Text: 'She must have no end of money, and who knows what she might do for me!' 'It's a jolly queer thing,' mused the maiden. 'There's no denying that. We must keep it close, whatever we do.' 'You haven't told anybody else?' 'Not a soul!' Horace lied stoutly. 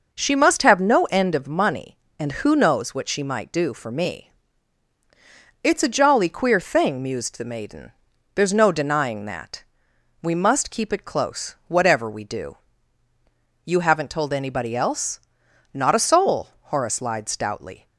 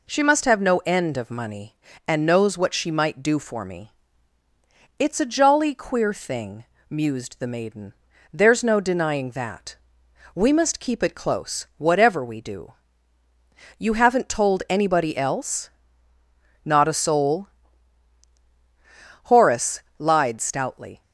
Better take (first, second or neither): first